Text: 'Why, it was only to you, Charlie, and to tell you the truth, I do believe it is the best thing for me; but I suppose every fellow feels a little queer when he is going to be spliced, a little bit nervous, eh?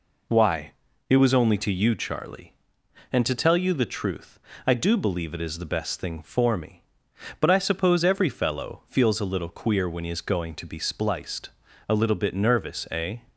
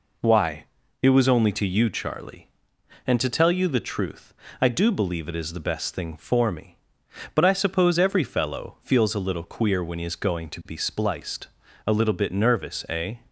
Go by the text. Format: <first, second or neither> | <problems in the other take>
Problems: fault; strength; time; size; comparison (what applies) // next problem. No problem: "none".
neither | none